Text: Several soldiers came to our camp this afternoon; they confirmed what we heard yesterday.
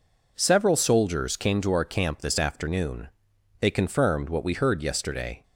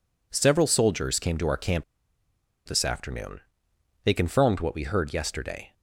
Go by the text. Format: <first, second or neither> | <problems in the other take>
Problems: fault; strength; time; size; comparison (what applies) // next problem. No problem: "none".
first | pauses between "camp" and "this"; noticeable; at 1.8 s; 0.83 s long